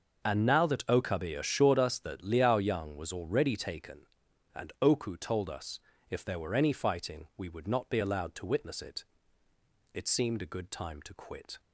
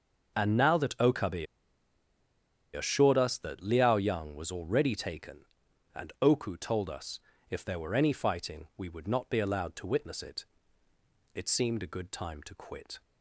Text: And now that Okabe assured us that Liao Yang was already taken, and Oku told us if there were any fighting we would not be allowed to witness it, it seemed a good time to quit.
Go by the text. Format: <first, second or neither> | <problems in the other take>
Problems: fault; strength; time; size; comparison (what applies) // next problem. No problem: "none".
first | pauses between "Okabe" and "assured"; strong; at 1.4 s; 1.2 s long // pauses between "us" and "if"; slight; at 7.1 s; 0.32 s long; slight in the first